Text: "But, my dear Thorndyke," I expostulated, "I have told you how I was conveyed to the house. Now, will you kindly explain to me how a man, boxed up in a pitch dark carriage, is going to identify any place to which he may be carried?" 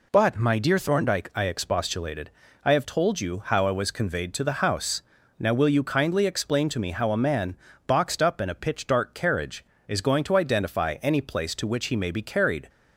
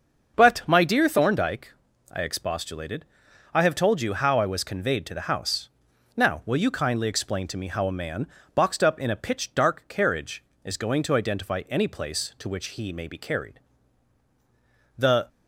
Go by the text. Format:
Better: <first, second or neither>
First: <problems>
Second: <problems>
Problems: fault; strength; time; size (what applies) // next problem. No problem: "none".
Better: first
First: none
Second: starts louder than the rest; until 1.3 s; 6.5 dB // goes on to say "The"; slight; from 14.9 s on; 0.32 s long